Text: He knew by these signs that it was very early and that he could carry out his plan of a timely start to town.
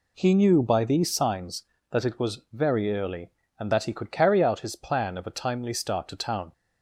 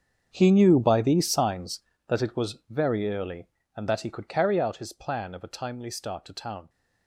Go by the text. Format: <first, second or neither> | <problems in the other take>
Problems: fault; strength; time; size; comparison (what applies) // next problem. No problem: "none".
first | gets quieter; strong; throughout; 16.5 dB